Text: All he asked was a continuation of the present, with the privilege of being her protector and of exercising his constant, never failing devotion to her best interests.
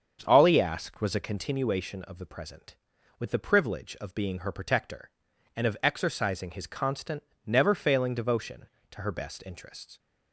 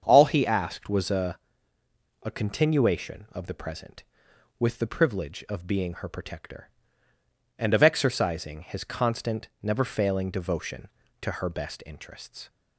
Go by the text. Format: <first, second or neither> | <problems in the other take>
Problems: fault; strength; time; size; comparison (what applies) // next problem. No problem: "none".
first | starts louder than the rest; until 1.0 s; 7 dB; also in the first // says "a" twice; at 2.2 s